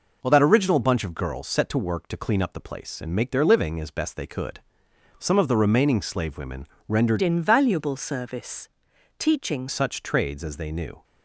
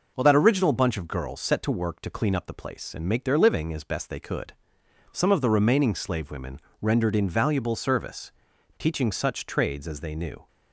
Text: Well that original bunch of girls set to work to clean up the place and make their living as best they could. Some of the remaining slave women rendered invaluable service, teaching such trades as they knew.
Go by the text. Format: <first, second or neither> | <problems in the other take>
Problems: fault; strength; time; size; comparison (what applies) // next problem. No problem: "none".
second | pauses between "women" and "rendered"; slight; at 6.6 s; 0.20 s long; slight in the second // changes voice from "invaluable" to "teaching"; from 7.2 to 9.6 s; 2.4 s long